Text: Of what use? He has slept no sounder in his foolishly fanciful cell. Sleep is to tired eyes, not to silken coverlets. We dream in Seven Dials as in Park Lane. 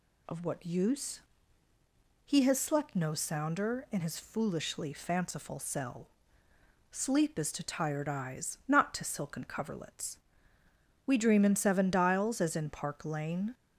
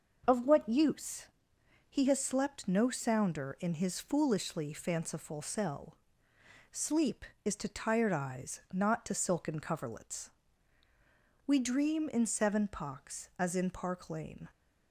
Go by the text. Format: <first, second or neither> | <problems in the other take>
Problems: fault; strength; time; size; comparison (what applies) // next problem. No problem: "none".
first | starts louder than the rest; noticeable; until 1.2 s; 6 dB // says "Pocks" for "Dials"; at 12.6 s